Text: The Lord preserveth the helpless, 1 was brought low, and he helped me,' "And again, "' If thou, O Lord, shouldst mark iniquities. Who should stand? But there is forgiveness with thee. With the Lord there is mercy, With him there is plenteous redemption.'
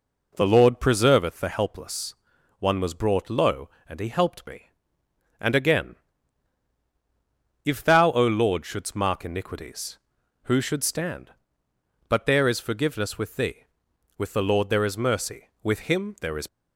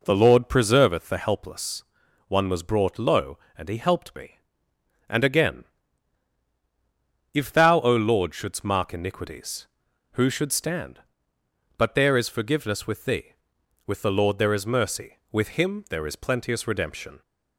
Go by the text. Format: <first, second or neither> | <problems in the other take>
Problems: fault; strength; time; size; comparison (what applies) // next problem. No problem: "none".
second | stops before "plenteous redemption"; at 16.4 s